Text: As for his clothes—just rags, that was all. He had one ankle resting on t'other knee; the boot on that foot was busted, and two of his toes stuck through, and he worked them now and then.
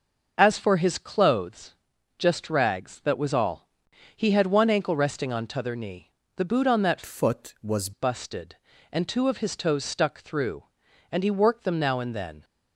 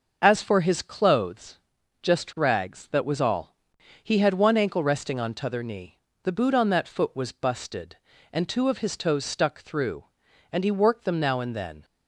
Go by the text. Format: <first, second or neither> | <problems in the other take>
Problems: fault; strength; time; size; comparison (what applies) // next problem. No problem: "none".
second | changes voice from "foot" to "was"; from 7.0 to 7.9 s; 0.9 s long